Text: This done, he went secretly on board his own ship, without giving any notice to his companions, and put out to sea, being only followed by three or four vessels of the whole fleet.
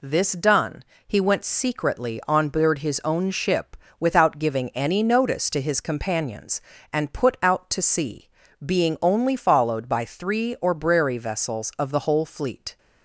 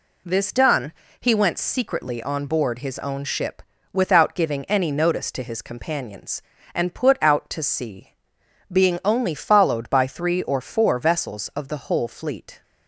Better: second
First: says "brary" for "four"; at 10.7 s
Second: none

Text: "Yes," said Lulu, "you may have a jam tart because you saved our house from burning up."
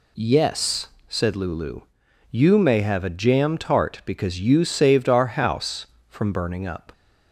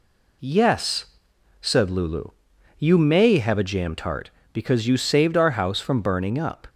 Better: neither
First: none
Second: none

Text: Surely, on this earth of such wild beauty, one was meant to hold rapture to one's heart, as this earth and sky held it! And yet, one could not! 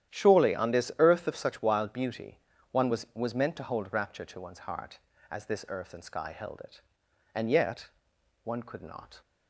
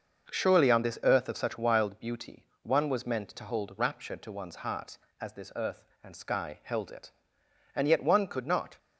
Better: second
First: starts louder than the rest; strong; until 1.1 s; 11 dB // says "was" twice; at 3.1 s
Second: starts louder than the rest; noticeable; until 1.3 s; 6 dB

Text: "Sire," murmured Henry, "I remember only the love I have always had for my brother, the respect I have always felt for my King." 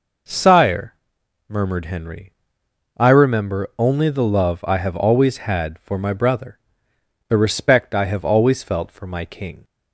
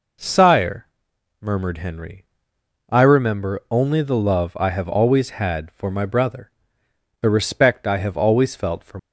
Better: first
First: none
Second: stops before "my King"; at 8.9 s

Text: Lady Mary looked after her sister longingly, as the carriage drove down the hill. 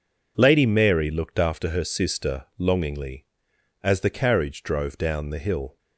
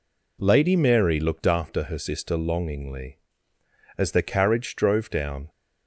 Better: first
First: none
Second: stops before "the hill"; at 5.4 s

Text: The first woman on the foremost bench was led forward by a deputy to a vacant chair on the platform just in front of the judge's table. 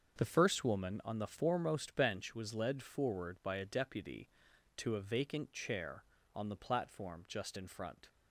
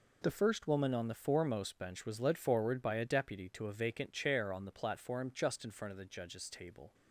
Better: second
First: starts louder than the rest; until 1.2 s; 6.5 dB // stops before "of the judge's table"; at 8.0 s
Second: none

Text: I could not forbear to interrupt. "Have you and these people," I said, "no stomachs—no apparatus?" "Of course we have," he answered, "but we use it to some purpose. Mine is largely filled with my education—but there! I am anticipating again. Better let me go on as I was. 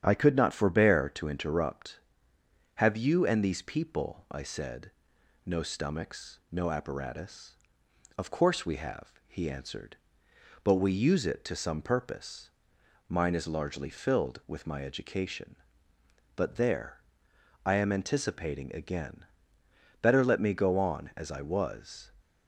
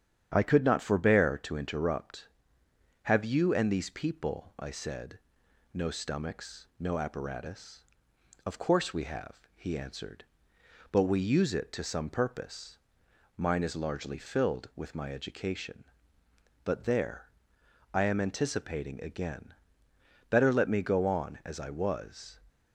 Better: neither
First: starts louder than the rest; strong; until 1.0 s; 9.5 dB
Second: starts louder than the rest; strong; until 1.3 s; 9.5 dB

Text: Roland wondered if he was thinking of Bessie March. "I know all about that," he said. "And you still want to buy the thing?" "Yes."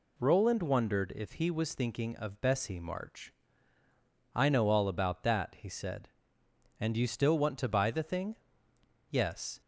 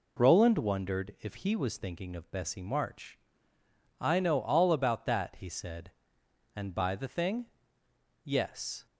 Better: first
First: none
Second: skips "you still want to"; at 6.7 s

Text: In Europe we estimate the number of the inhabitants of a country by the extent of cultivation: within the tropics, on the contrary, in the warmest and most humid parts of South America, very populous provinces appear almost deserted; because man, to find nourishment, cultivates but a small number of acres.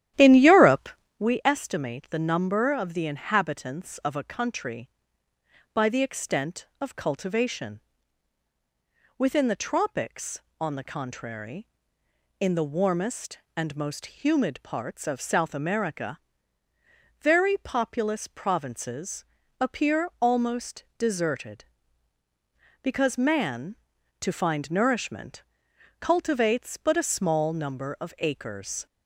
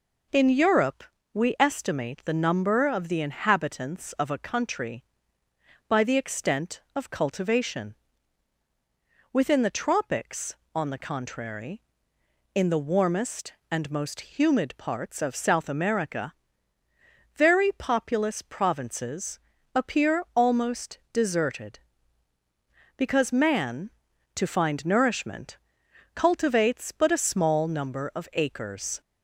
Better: second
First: starts louder than the rest; strong; until 1.3 s; 12 dB // pauses between "Europe" and "we"; slight; at 0.8 s; 0.28 s long // pauses between "provinces" and "appear"; slight; at 19.2 s; 0.36 s long // pauses between "almost" and "deserted"; slight; at 20.8 s; 0.16 s long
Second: pauses between "Europe" and "we"; slight; at 1.0 s; 0.28 s long // pauses between "provinces" and "appear"; slight; at 19.3 s; 0.36 s long // pauses between "almost" and "deserted"; slight; at 20.9 s; 0.16 s long

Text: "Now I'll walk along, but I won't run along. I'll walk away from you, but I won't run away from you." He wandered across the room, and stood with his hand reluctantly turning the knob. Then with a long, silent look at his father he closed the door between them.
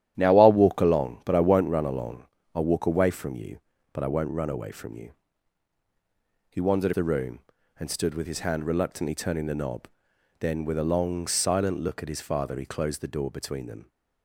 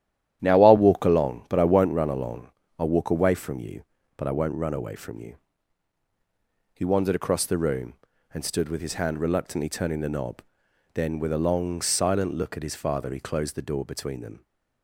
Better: second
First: starts louder than the rest; strong; until 1.1 s; 11.5 dB // skips "across"; at 6.9 s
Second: starts louder than the rest; strong; until 1.4 s; 11.5 dB

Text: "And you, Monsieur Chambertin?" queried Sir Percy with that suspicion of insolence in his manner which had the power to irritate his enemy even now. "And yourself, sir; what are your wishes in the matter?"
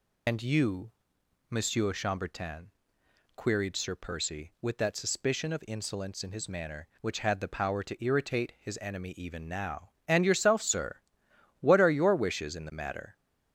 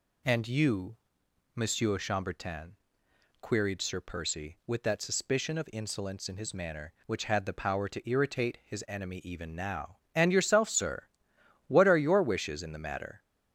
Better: second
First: loses the start of "And"; at 0.2 s; 70 ms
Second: none

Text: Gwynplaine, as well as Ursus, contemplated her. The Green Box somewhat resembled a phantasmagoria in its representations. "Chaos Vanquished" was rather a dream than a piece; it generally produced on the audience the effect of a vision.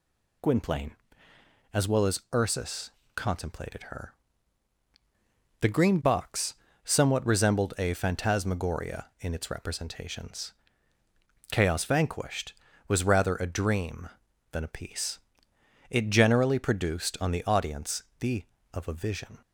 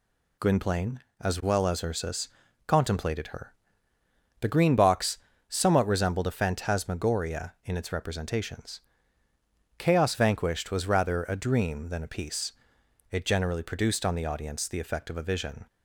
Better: second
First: pauses between "Box" and "somewhat"; slight; at 6.5 s; 0.28 s long // pauses between "audience" and "the"; slight; at 18.0 s; 0.16 s long // skips "effect"; at 18.5 s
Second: pauses between "Box" and "somewhat"; slight; at 5.1 s; 0.30 s long

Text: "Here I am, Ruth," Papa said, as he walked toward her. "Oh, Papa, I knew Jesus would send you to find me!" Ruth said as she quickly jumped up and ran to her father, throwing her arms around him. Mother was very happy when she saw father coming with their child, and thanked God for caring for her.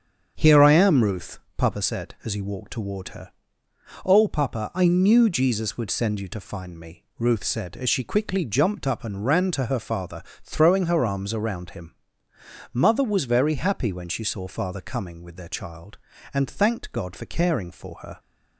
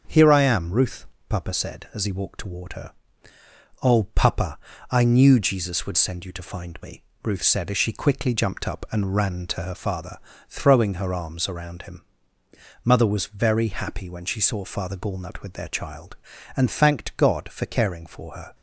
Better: first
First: starts louder than the rest; strong; until 1.3 s; 7 dB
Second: starts louder than the rest; until 1.3 s; 6.5 dB // says "gallnut" for "coming"; at 14.9 s

